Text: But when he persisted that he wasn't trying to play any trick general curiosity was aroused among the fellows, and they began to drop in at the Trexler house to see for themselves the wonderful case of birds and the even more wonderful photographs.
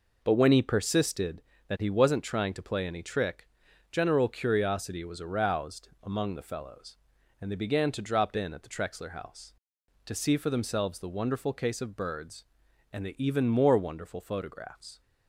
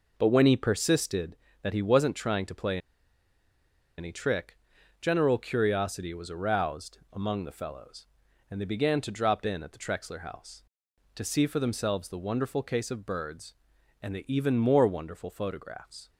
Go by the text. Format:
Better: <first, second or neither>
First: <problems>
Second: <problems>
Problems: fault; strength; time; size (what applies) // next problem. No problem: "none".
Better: first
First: pauses between "trick" and "general"; at 3.4 s; 0.42 s long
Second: pauses between "play" and "any"; at 2.7 s; 1.1 s long // pauses between "trick" and "general"; at 4.5 s; 0.42 s long